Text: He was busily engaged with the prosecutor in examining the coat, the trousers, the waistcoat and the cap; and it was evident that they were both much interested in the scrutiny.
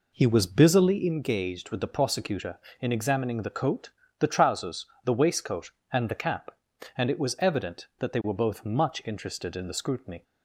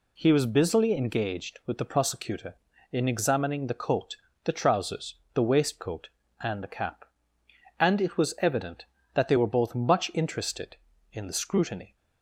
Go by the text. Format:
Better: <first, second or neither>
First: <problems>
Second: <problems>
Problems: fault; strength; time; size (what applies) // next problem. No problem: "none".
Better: second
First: starts louder than the rest; until 1.2 s; 4 dB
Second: none